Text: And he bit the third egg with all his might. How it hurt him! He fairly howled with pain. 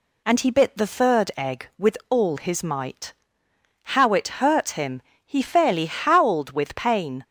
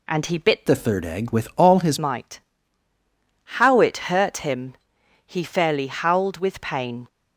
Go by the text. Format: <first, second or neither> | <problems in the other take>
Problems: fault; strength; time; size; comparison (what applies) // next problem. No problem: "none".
first | changes voice from "the" to "his"; from 0.6 to 1.9 s; 1.3 s long